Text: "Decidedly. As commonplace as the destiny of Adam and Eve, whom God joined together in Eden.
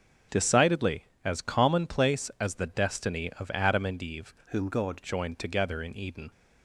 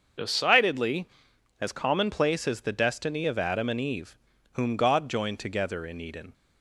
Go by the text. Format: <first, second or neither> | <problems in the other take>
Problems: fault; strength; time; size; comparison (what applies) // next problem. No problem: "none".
second | starts louder than the rest; strong; until 1.4 s; 8 dB; also in the second // changes voice from "whom" to "God"; from 4.5 to 5.0 s; 0.5 s long